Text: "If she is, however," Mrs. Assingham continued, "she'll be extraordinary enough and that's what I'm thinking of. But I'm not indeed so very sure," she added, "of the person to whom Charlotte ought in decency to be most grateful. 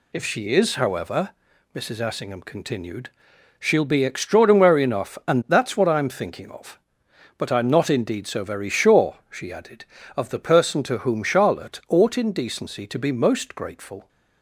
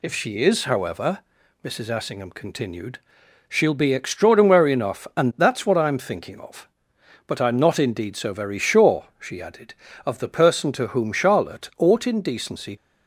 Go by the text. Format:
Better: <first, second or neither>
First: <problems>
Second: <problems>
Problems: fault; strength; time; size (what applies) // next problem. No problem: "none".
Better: first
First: none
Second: stops before "to be most grateful"; at 12.7 s